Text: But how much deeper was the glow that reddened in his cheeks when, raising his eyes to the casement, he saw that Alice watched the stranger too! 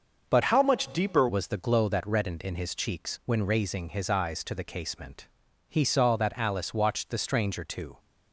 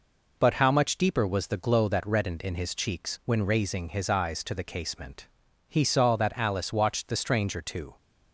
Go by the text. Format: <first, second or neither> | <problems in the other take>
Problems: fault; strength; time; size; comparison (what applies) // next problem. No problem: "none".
second | starts louder than the rest; until 1.3 s; 6.5 dB // changes voice from "how" to "deeper"; from 0.4 to 1.2 s; 0.8 s long